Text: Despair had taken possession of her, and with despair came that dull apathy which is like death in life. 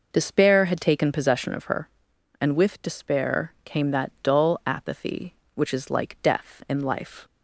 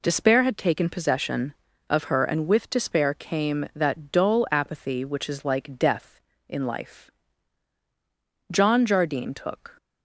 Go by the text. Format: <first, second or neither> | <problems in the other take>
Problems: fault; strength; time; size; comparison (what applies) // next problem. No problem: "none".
first | goes on to say "John Jardine took"; noticeable; from 8.5 s on; 1.2 s long